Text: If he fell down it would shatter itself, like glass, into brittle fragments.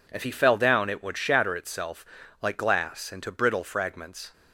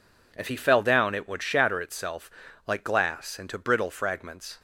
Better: neither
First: none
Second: none

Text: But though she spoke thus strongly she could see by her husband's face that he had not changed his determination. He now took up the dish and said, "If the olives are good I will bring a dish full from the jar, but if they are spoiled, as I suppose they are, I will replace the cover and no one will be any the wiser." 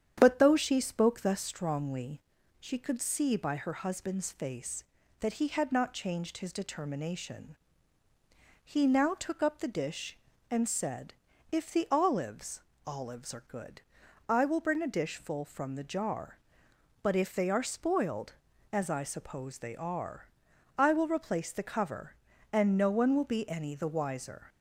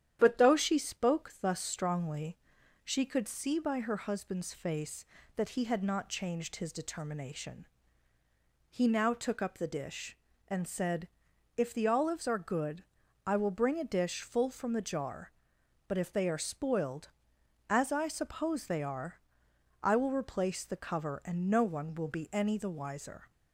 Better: second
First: starts louder than the rest; strong; until 1.1 s; 9 dB // pauses between "strongly" and "she"; at 2.2 s; 0.38 s long // says "olives" twice; at 12.8 s // pauses between "good" and "I"; noticeable; at 13.8 s; 0.48 s long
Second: starts louder than the rest; strong; until 1.2 s; 10 dB // pauses between "strongly" and "she"; noticeable; at 2.3 s; 0.48 s long // pauses between "good" and "I"; at 12.8 s; 0.42 s long

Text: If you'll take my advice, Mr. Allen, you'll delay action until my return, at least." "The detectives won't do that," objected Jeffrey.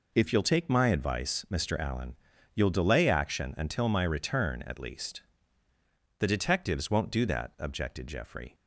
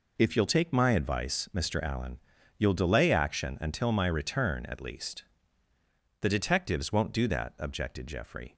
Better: neither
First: none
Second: none

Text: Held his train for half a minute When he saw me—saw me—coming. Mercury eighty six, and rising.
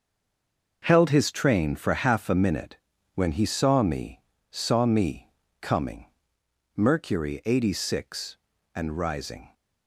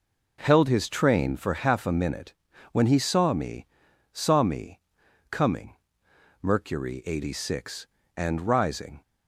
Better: second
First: stays silent before the first word; slight; until 0.8 s; 0.8 s long // pauses between "minute" and "When"; at 2.7 s; 0.40 s long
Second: pauses between "minute" and "When"; at 2.3 s; 0.40 s long

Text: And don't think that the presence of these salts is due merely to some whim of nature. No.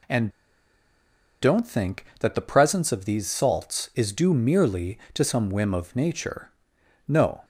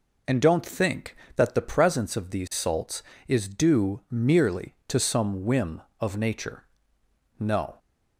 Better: second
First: pauses between "And" and "don't"; at 0.2 s; 1.1 s long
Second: none

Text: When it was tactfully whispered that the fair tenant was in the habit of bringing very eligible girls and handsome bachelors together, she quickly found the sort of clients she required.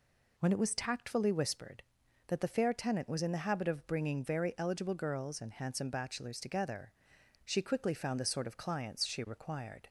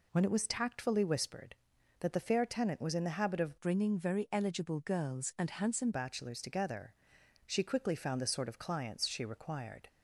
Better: first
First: none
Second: changes voice from "bringing" to "handsome"; from 3.6 to 5.9 s; 2.3 s long

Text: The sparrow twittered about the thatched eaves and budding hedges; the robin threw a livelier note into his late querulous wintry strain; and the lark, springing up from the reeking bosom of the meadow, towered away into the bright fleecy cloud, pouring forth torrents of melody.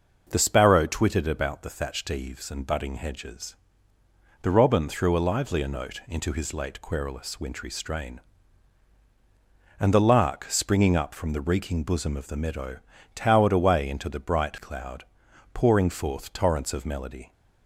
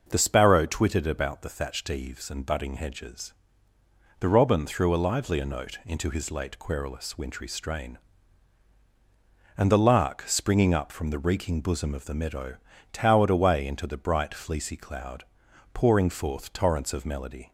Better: second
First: skips "fleecy"; at 14.5 s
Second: none

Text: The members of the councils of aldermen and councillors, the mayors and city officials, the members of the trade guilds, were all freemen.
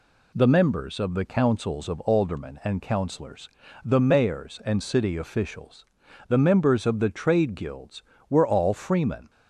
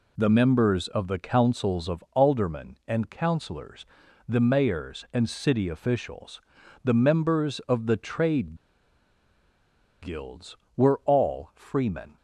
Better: first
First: none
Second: pauses between "trade" and "guilds"; strong; at 8.5 s; 1.4 s long

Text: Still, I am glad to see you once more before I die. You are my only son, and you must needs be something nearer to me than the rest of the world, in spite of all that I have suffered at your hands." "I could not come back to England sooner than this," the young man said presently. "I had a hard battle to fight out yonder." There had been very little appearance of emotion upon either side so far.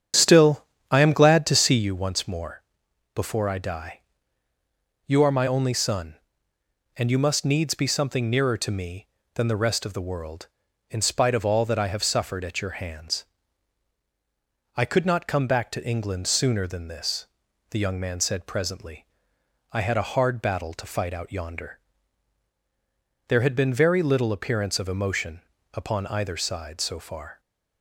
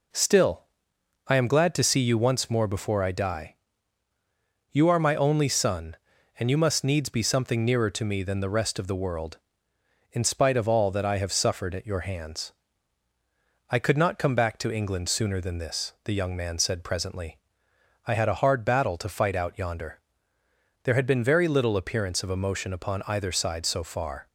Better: second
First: starts louder than the rest; strong; until 2.0 s; 8.5 dB // pauses between "more" and "before"; noticeable; at 2.6 s; 0.52 s long // pauses between "emotion" and "upon"; slight; at 25.4 s; 0.32 s long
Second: none

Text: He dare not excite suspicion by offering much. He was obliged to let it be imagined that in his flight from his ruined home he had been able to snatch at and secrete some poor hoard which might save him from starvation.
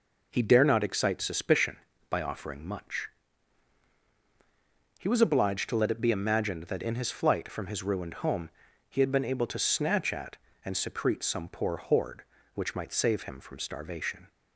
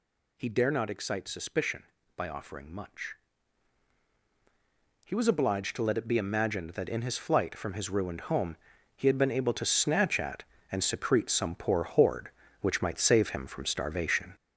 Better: first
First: pauses between "home" and "he"; at 8.4 s; 0.40 s long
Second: gets louder; noticeable; throughout; 5.5 dB // pauses between "home" and "he"; at 8.5 s; 0.40 s long

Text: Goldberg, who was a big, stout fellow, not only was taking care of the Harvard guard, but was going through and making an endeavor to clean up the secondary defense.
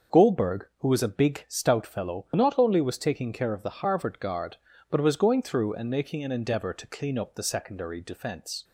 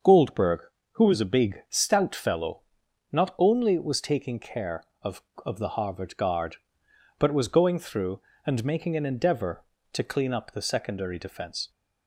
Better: first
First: starts louder than the rest; until 1.2 s; 6.5 dB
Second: starts louder than the rest; until 1.3 s; 6.5 dB // says "of" twice; at 5.4 s

